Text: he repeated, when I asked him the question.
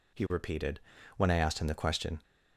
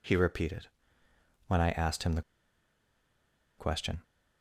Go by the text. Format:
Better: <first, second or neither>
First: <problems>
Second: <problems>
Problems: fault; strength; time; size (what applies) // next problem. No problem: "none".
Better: first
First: none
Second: pauses between "the" and "question"; strong; at 2.2 s; 1.3 s long